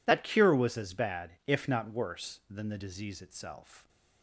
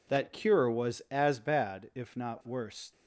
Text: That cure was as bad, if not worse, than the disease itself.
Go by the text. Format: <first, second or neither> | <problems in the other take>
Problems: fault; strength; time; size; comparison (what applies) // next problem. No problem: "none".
first | stops before "than the disease itself"; at 2.9 s